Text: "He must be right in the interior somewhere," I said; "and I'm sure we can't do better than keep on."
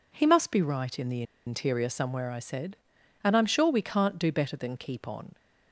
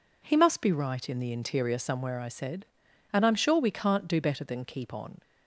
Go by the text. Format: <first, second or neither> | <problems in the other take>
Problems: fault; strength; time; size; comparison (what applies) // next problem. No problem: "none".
second | pauses between "the" and "interior"; slight; at 1.2 s; 0.23 s long